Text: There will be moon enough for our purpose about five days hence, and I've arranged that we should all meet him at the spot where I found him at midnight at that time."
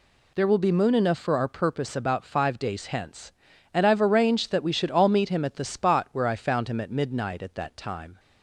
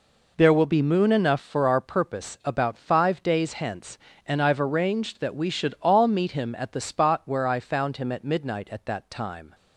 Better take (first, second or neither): neither